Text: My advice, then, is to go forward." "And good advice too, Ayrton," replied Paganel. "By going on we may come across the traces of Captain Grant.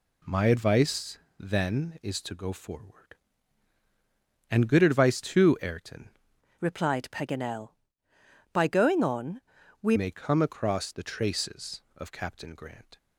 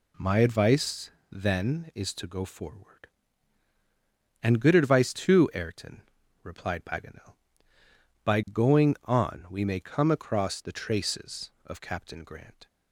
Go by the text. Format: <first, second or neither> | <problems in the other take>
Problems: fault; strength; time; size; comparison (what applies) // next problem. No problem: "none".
second | changes voice from "replied" to "we"; from 6.6 to 9.9 s; 3.3 s long // pauses between "on" and "we"; at 9.4 s; 0.40 s long